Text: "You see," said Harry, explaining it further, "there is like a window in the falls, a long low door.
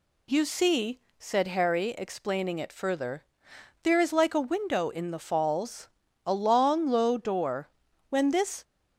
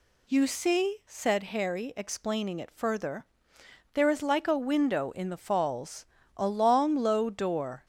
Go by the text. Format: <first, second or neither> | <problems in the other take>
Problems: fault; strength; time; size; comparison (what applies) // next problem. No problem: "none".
second | goes on to say "When this"; from 8.1 s on; 0.52 s long